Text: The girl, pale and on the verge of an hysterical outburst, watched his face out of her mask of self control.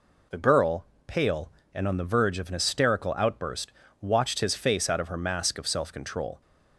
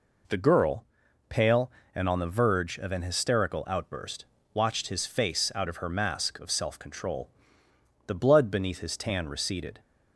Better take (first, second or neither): first